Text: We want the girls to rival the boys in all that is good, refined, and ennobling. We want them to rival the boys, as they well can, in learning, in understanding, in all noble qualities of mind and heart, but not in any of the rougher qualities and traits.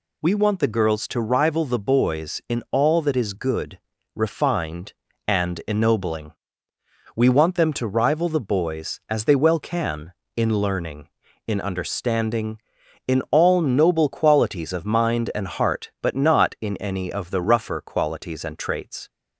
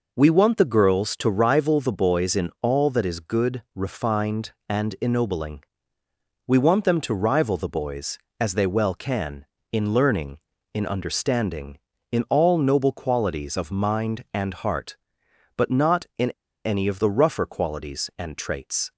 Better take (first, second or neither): first